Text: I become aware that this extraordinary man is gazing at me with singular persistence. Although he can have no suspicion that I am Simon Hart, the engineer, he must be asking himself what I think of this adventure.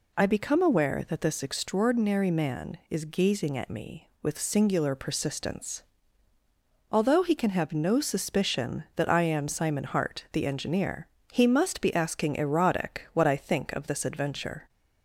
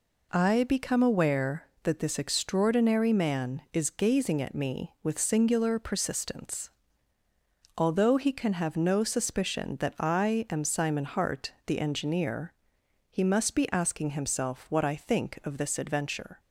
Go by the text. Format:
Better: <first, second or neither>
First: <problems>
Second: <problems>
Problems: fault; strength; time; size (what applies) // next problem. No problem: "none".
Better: second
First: says "erotic" for "himself"; at 12.3 s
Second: none